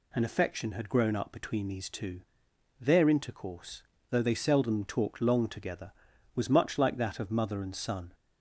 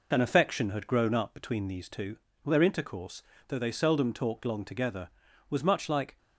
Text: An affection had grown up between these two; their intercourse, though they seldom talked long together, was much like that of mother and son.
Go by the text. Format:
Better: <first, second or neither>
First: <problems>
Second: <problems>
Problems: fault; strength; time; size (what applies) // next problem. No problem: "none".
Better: first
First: none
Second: stops before "that of mother and son"; at 6.1 s